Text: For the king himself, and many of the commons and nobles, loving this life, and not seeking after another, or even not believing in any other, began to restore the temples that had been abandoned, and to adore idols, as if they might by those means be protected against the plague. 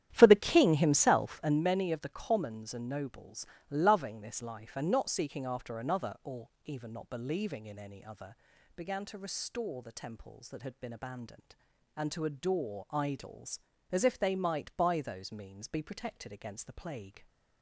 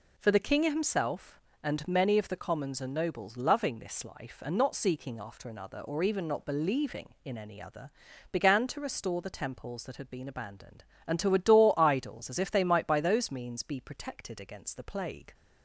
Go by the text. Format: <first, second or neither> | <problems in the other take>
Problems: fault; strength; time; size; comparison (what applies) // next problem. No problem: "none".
second | starts louder than the rest; strong; until 1.7 s; 10.5 dB // pauses between "or" and "even"; slight; at 6.4 s; 0.16 s long